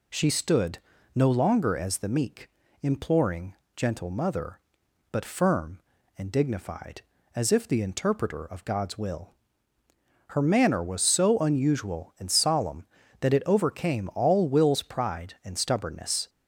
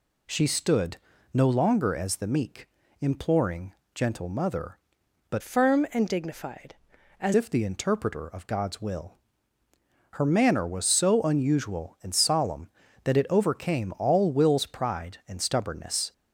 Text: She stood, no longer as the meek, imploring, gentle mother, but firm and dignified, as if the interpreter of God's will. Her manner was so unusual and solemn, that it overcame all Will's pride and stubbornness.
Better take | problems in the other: first | changes voice from "firm" to "as"; from 5.4 to 7.3 s; 1.9 s long

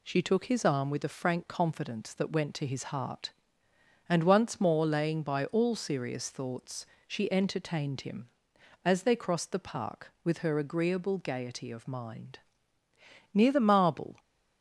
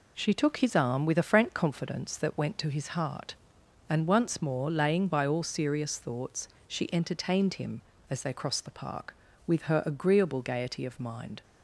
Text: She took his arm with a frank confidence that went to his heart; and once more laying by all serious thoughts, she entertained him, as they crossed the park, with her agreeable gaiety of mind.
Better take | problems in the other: second | goes on to say "Near the Marble"; noticeable; from 13.3 s on; 0.86 s long

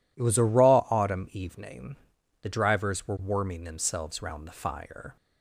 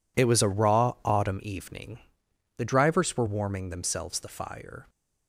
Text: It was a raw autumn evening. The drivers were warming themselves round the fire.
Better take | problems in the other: first | skips "round"; at 4.1 s

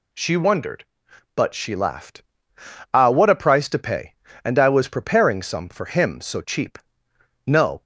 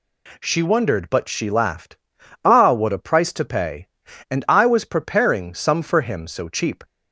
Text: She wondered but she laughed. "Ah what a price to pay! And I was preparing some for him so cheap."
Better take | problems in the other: second | goes on to say "No"; slight; from 7.4 s on; 0.36 s long

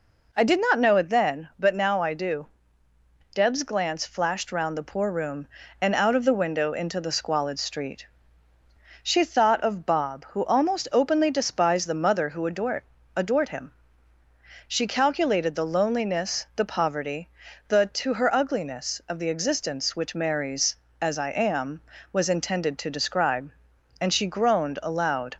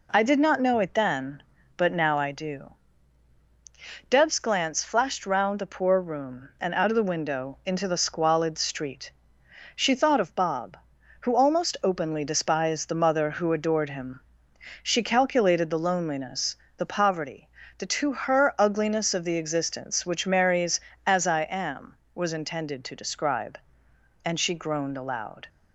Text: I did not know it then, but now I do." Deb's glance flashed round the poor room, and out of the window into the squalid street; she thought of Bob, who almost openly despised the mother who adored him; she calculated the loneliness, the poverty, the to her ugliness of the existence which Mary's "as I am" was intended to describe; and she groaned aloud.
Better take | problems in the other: second | says "adored" twice; at 13.1 s

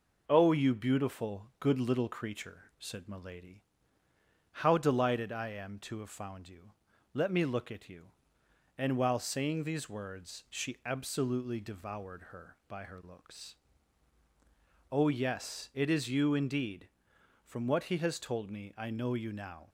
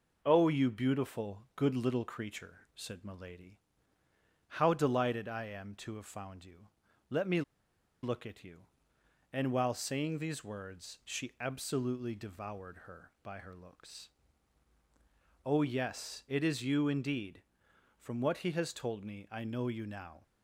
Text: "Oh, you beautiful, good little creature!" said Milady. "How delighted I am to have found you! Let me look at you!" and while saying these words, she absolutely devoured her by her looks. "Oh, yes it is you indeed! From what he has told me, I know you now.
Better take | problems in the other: first | pauses between "me" and "look"; noticeable; at 7.4 s; 0.61 s long

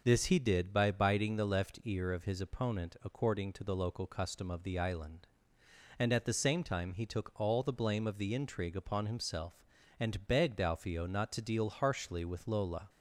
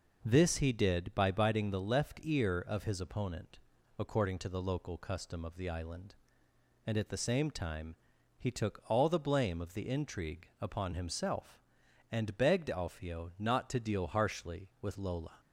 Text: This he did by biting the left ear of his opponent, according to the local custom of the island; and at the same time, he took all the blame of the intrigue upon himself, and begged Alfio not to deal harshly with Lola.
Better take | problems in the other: neither | none

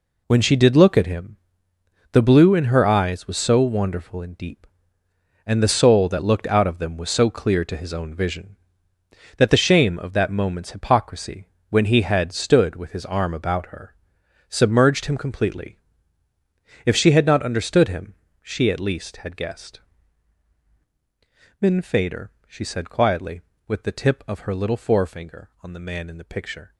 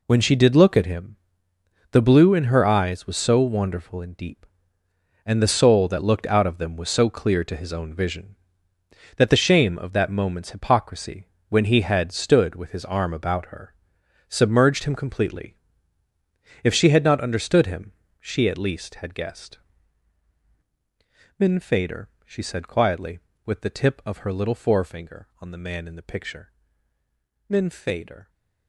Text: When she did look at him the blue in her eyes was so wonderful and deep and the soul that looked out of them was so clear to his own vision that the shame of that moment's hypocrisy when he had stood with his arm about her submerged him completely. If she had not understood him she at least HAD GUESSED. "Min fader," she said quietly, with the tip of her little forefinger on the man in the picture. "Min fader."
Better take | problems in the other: second | pauses between "him" and "the"; noticeable; at 1.3 s; 0.74 s long; noticeable in the second // pauses between "hypocrisy" and "when"; slight; at 11.4 s; 0.22 s long; slight in the second // pauses between "her" and "submerged"; noticeable; at 13.9 s; 0.52 s long; noticeable in the second // pauses between "him" and "she"; slight; at 18.1 s; 0.32 s long; slight in the second // stops before "Min fader"; at 26.7 s

